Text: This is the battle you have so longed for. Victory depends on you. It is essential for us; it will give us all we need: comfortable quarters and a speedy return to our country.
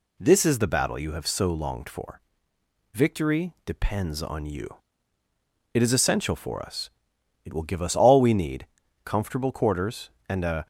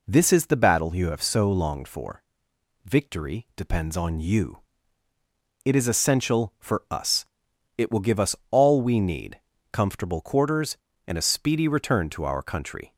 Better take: second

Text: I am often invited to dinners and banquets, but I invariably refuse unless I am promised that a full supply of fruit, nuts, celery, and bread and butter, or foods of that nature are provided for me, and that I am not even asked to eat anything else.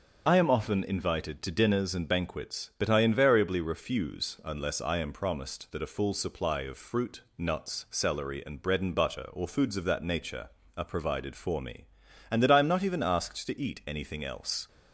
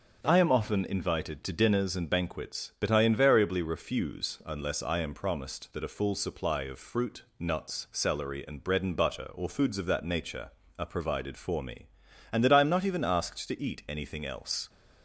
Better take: second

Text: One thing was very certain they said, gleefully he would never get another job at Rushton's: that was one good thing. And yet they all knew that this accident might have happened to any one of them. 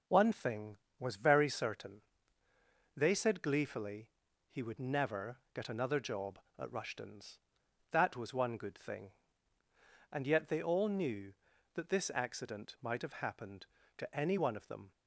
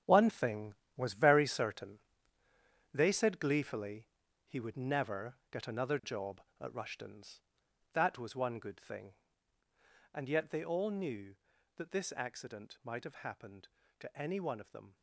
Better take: first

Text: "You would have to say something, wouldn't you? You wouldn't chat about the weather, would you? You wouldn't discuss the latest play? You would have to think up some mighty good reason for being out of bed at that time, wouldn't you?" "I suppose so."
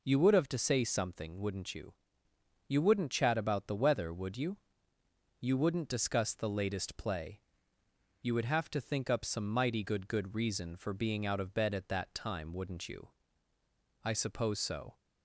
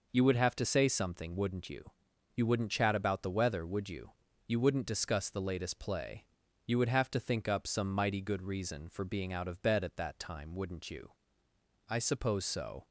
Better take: second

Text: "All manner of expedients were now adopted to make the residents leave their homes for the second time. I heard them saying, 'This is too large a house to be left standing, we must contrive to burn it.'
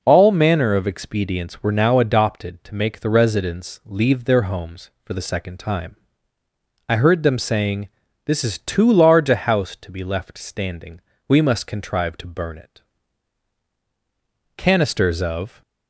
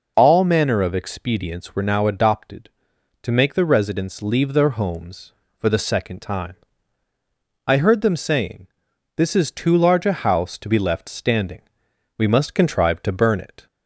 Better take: second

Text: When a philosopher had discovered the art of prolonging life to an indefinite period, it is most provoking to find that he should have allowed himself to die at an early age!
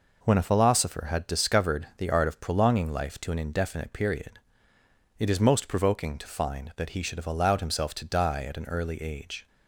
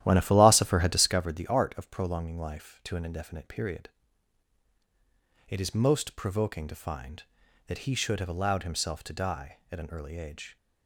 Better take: first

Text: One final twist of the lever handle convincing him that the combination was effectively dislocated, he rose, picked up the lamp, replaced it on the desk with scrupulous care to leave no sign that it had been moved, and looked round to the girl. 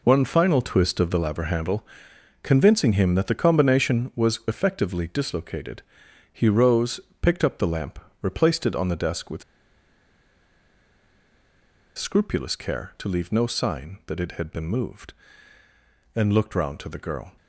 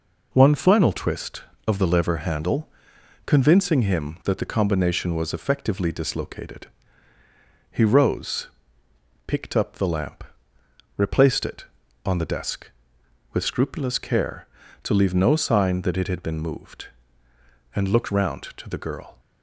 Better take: second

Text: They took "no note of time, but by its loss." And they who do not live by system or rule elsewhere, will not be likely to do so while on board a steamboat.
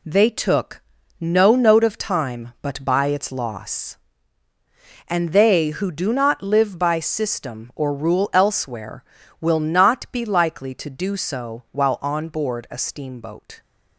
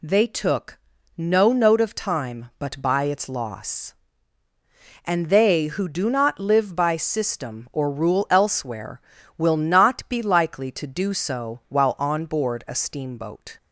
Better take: second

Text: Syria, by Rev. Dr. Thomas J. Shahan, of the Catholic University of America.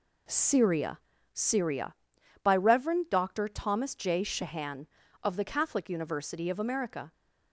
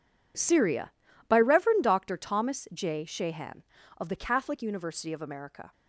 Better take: second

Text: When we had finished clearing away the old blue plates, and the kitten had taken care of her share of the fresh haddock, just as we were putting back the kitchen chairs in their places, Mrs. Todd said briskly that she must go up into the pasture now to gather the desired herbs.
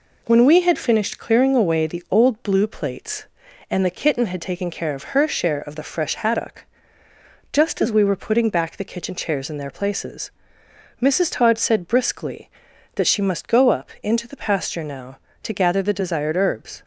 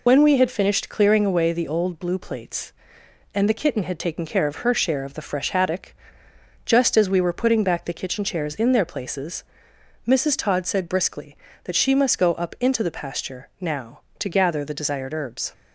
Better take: first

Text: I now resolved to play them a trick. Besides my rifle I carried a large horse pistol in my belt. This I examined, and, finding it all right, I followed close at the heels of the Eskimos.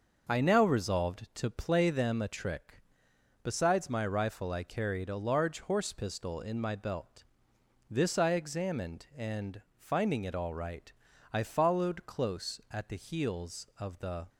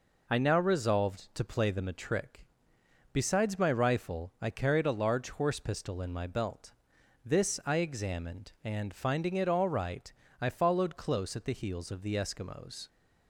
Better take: second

